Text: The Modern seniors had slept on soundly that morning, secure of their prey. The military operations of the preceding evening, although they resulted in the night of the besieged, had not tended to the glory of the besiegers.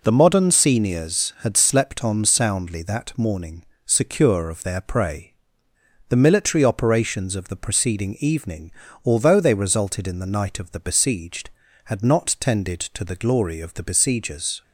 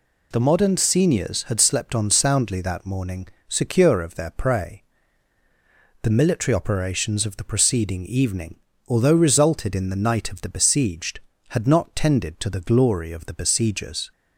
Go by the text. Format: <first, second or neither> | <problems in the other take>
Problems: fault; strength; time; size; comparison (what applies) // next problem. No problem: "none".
first | skips "they"; at 9.1 s